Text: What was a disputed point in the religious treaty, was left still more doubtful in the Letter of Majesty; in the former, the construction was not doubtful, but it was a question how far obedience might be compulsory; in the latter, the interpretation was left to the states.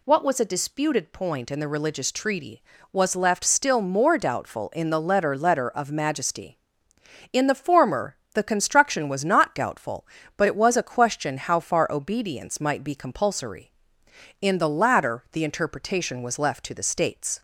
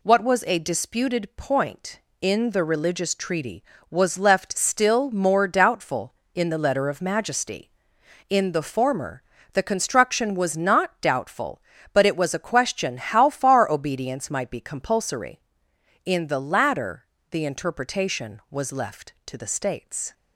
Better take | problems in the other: second | says "Letter" twice; at 5.3 s

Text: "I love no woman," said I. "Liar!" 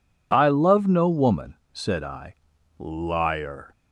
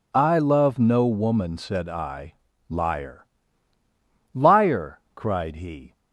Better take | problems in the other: first | goes on to say "Liar cried he"; from 4.3 s on; 1.5 s long

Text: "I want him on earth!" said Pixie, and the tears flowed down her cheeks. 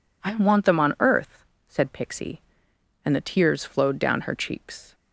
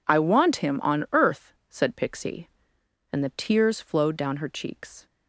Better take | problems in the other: second | says "them" for "him"; at 0.6 s

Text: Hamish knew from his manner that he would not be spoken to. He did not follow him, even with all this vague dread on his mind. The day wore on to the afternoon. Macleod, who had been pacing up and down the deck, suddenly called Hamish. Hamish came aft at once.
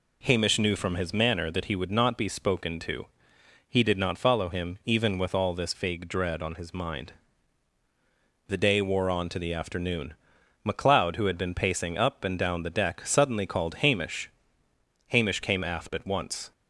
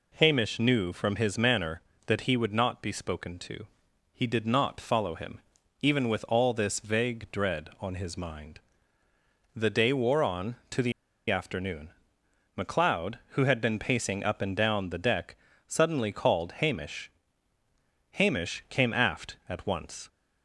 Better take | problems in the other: first | pauses between "the" and "afternoon"; at 10.9 s; 0.38 s long

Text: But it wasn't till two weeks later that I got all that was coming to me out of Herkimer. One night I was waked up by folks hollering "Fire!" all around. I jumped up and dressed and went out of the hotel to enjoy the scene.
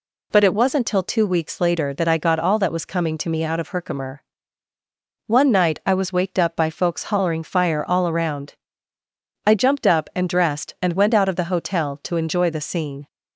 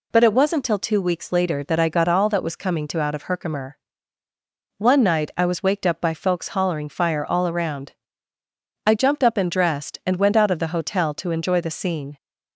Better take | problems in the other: first | skips "me"; at 3.0 s

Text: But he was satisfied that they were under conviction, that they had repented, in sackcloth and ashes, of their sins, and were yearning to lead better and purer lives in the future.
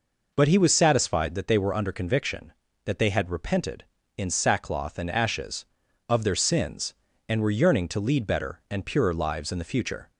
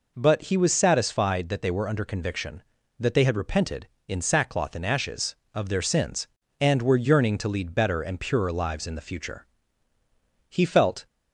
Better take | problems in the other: first | goes on to say "He felt"; from 10.4 s on; 0.58 s long

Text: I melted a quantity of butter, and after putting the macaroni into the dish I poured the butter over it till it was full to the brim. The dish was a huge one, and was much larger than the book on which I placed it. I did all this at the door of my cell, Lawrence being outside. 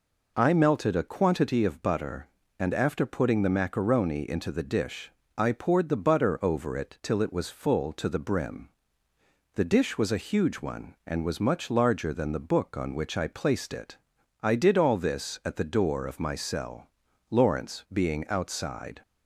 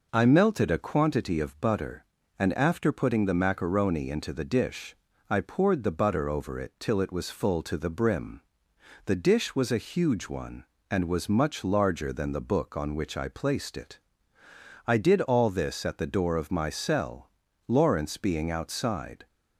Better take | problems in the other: neither | pauses between "dish" and "I"; slight; the same in both

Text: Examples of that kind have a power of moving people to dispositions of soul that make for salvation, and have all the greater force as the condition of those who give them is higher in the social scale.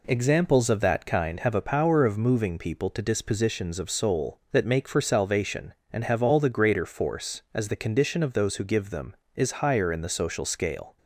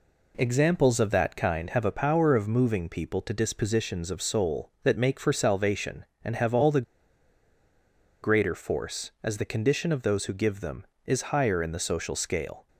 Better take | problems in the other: first | pauses between "the" and "greater"; strong; at 6.8 s; 1.4 s long

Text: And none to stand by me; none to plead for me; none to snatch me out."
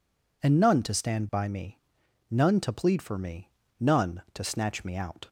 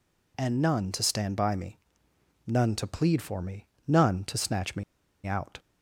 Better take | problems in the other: first | pauses between "me" and "out"; at 4.8 s; 0.41 s long

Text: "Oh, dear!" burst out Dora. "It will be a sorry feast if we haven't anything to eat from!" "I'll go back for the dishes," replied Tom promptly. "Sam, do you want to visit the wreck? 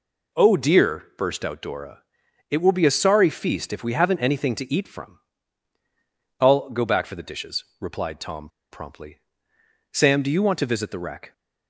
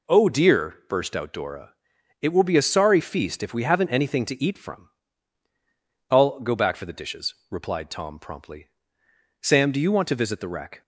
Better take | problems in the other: second | pauses between "Tom" and "promptly"; slight; at 8.4 s; 0.23 s long

